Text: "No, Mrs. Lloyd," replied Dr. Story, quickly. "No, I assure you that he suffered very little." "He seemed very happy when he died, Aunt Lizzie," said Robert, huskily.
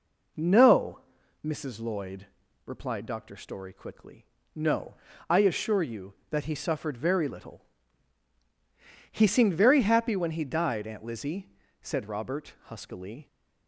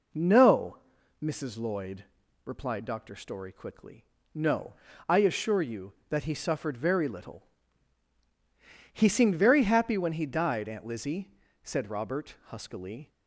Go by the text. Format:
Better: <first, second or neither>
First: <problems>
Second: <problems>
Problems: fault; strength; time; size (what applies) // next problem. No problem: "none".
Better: neither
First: none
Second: none